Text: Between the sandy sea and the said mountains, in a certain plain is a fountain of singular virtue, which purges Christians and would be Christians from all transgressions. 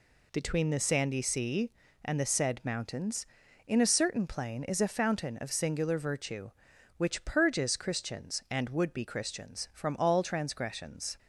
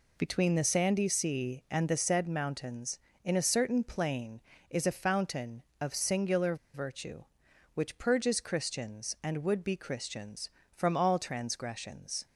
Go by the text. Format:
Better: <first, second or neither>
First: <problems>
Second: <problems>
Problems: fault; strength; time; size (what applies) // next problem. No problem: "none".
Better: first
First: none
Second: pauses between "singular" and "virtue"; slight; at 6.5 s; 0.18 s long